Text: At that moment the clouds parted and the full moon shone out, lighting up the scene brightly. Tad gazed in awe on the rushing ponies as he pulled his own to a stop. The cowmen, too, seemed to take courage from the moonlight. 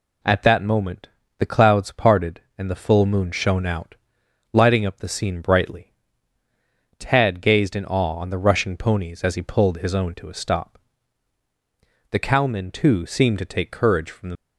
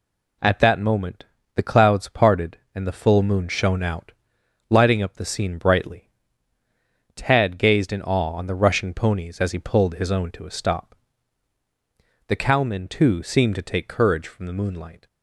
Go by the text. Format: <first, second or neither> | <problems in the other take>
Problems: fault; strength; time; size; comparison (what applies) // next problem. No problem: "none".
second | pauses between "moment" and "the"; slight; at 1.0 s; 0.32 s long; slight in the second // stops before "moonlight"; at 14.3 s